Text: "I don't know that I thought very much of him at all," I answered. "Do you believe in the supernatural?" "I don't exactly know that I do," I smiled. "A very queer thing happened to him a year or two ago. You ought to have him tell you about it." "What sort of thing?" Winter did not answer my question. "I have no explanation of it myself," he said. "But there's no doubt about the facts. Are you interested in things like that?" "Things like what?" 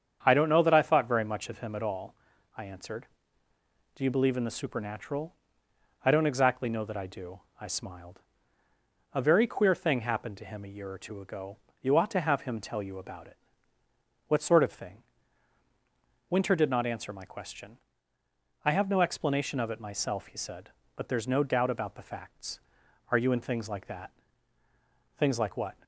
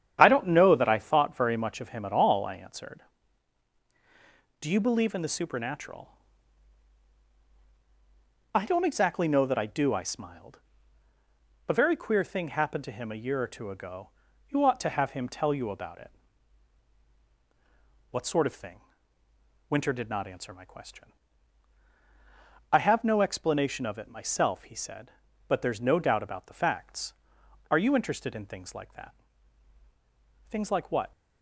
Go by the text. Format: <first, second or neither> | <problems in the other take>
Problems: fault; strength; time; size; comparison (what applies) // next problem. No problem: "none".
second | starts louder than the rest; strong; until 1.2 s; 7.5 dB; strong in the second // skips "interested"; at 23.3 s